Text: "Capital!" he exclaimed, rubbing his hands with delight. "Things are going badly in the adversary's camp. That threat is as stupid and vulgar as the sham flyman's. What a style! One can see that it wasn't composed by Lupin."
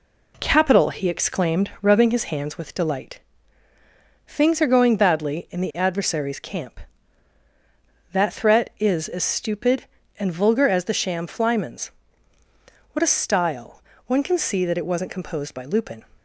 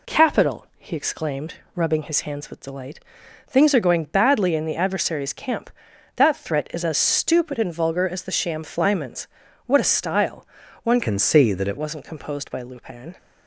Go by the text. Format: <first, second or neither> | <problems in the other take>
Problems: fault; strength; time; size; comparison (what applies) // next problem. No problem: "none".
first | changes voice from "can" to "it"; from 11.0 to 11.7 s; 0.7 s long